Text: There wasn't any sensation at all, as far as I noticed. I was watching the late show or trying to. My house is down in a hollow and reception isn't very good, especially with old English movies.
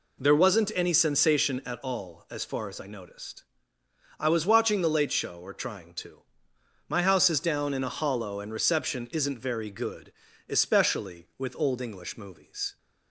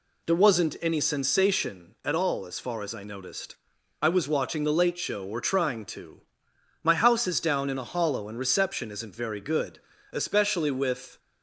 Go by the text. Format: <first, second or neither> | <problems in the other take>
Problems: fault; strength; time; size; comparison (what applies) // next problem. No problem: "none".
first | stops before "old English movies"; at 11.1 s